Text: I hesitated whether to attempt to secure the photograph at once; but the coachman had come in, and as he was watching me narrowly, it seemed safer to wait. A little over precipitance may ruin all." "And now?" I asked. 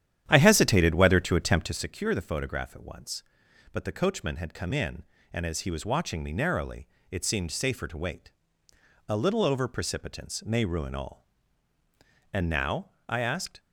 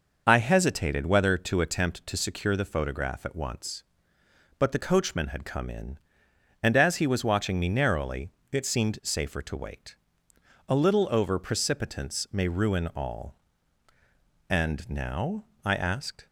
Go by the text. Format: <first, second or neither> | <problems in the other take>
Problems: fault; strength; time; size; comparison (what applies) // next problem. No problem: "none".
second | starts louder than the rest; strong; until 1.9 s; 10.5 dB